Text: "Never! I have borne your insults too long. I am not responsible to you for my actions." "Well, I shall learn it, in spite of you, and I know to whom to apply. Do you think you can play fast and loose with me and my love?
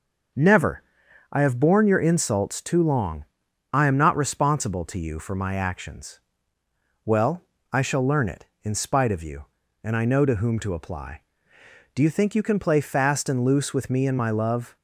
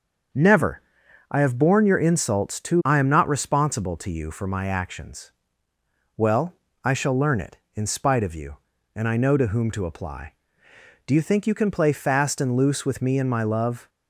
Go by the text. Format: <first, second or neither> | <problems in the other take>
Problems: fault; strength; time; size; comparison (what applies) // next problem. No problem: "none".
first | starts louder than the rest; until 1.8 s; 6.5 dB; noticeable in the first // skips "long"; at 2.8 s